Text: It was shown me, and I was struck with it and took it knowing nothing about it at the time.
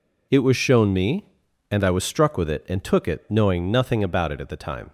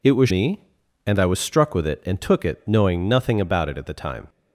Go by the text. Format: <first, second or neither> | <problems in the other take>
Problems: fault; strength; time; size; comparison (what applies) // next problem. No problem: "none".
first | skips "shown"; at 0.2 s